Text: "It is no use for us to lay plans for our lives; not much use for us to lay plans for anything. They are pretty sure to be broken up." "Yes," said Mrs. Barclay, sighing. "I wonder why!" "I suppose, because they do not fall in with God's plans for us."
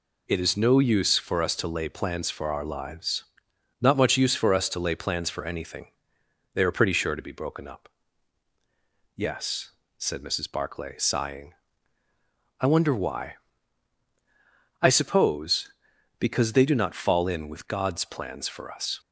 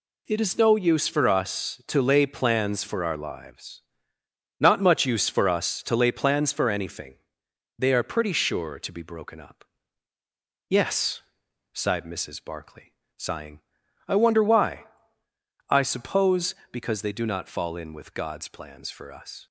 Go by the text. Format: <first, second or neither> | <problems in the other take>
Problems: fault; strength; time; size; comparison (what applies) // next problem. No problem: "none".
first | says "sighed" for "said"; at 11.7 s